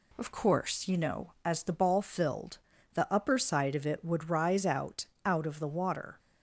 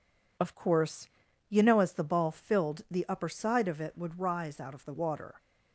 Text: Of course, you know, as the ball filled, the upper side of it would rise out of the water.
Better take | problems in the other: second | says "out" twice; at 5.2 s

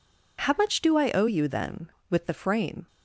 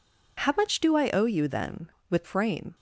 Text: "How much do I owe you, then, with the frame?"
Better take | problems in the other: first | skips "the"; at 2.2 s

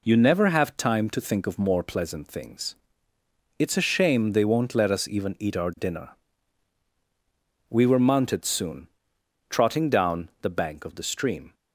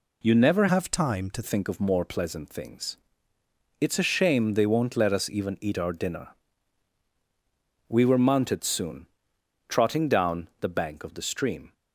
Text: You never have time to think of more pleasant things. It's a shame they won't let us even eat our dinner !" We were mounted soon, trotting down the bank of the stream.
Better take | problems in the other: first | changes voice from "have" to "to"; from 0.6 to 1.4 s; 0.8 s long

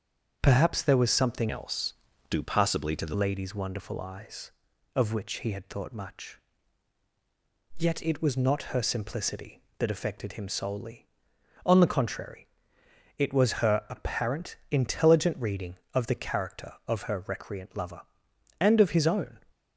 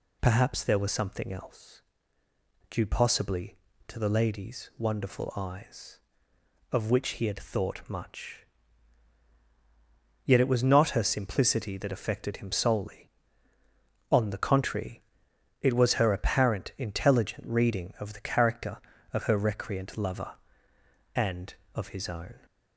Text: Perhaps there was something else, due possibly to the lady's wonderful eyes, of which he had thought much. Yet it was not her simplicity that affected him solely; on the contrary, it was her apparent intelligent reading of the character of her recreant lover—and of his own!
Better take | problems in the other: second | starts louder than the rest; strong; until 1.4 s; 7 dB // changes voice from "else" to "the"; from 1.4 to 3.1 s; 1.7 s long

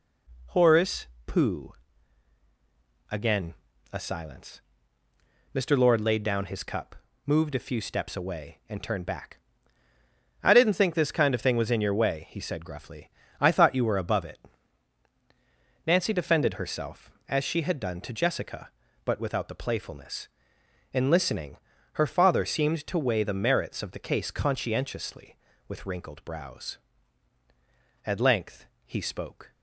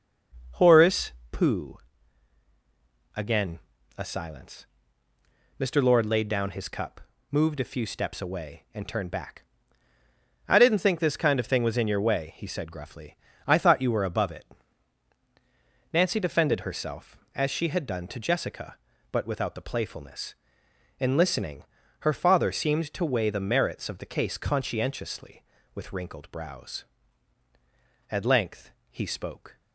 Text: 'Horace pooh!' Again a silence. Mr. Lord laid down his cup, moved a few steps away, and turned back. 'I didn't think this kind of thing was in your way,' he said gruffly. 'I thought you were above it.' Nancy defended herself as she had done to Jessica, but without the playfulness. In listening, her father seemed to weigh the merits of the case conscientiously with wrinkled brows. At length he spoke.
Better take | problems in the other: first | starts louder than the rest; noticeable; until 1.5 s; 6 dB // pauses between "Horace" and "pooh"; slight; at 1.1 s; 0.20 s long; slight in the first // pauses between "Again" and "a"; at 3.5 s; 0.38 s long; also in the first // pauses between "length" and "he"; slight; at 28.7 s; 0.18 s long; slight in the first

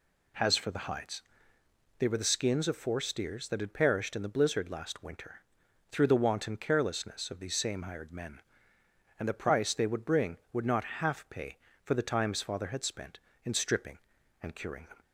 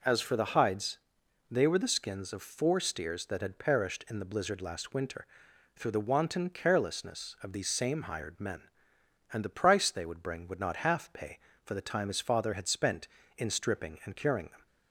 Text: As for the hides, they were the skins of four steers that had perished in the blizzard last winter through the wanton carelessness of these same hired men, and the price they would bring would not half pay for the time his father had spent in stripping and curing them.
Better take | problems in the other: second | says "Has" for "As"; at 0.3 s // pauses between "winter" and "through"; noticeable; at 5.3 s; 0.58 s long; noticeable in the second

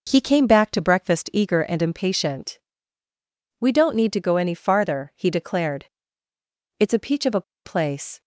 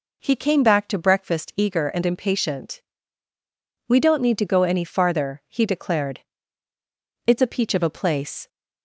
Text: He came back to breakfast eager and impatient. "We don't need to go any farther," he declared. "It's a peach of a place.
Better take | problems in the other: second | pauses between "a" and "place"; slight; at 7.4 s; 0.23 s long

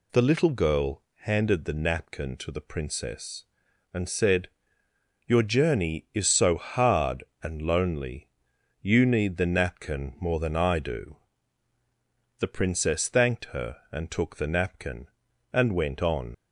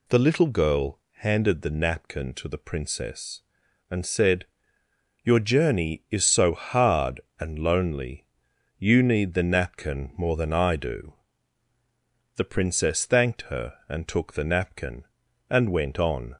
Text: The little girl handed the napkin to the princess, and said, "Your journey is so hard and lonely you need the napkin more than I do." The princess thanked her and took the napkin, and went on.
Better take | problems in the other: second | pauses between "girl" and "handed"; slight; at 1.0 s; 0.18 s long; slight in the second // pauses between "lonely" and "you"; noticeable; at 8.2 s; 0.54 s long; noticeable in the second // leaves "on" unfinished; at 16.3 s; 50 ms

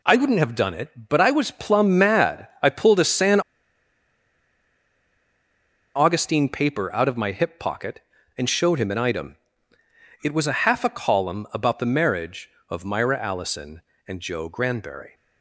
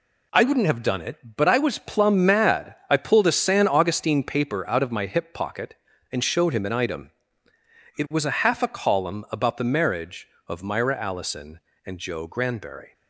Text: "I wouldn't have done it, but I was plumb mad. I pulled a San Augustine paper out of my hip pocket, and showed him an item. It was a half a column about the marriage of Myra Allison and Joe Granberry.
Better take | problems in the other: second | pauses between "San" and "Augustine"; strong; at 3.3 s; 2.5 s long

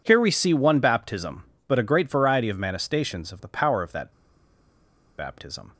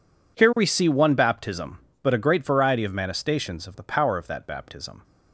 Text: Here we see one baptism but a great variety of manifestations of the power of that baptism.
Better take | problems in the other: second | pauses between "that" and "baptism"; at 4.1 s; 1.0 s long

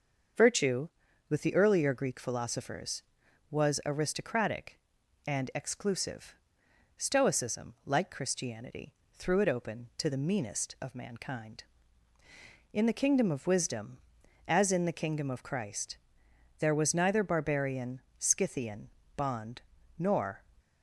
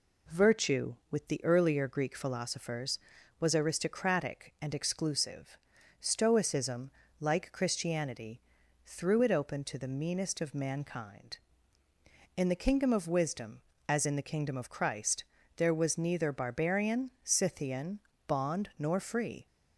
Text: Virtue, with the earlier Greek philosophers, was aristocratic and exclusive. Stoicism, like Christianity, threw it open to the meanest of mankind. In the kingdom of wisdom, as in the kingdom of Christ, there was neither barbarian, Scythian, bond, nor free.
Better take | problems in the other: second | starts louder than the rest; until 1.7 s; 6.5 dB // stops before "free"; at 20.5 s

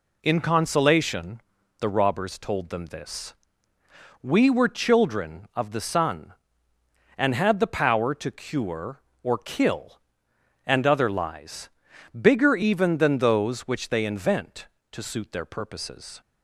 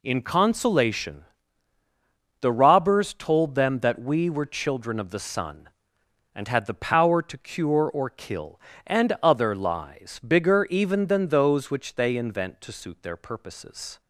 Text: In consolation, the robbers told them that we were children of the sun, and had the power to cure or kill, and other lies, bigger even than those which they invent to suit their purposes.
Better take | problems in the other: second | says "this" for "that"; at 2.8 s

